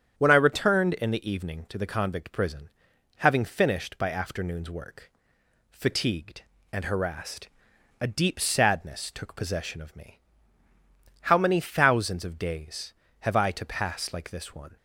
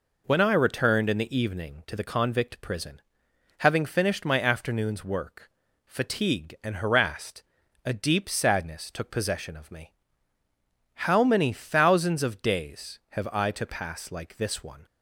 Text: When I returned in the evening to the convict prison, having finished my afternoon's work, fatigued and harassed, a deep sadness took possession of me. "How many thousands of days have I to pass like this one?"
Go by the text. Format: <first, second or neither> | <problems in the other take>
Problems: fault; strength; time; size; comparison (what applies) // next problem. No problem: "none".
second | starts louder than the rest; strong; until 1.1 s; 8.5 dB // says "by" for "my"; at 3.9 s